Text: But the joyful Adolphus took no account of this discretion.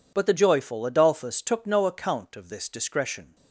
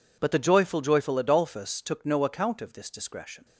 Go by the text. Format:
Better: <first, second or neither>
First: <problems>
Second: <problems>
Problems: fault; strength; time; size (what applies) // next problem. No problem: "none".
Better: first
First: none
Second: says "joyful" twice; at 0.8 s